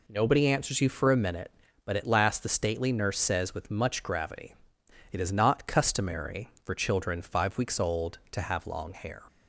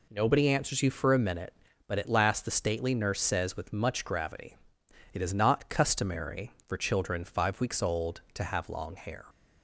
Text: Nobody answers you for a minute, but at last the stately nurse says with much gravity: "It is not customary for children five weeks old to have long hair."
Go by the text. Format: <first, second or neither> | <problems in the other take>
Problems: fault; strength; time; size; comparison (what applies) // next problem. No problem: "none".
neither | none